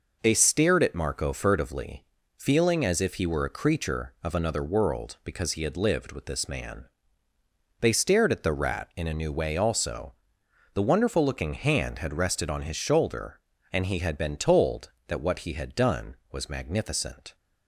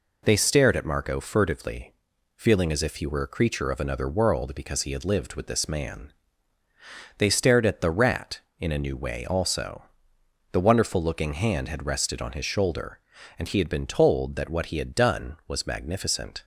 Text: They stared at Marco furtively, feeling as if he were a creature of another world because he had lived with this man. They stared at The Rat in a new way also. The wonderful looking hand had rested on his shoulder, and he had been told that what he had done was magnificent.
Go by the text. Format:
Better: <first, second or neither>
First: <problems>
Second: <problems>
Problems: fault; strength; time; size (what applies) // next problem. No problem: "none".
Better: neither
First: none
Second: none